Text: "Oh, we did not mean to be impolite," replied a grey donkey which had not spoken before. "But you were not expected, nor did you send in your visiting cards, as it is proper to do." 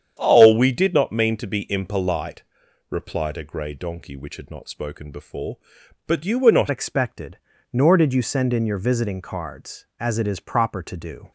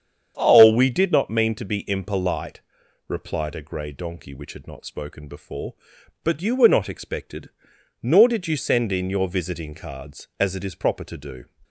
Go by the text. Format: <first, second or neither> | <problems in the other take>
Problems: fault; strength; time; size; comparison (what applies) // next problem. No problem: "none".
second | starts louder than the rest; strong; until 1.1 s; 8.5 dB; strong in the second // changes voice at "expected"; from 6.7 s on; 4.6 s long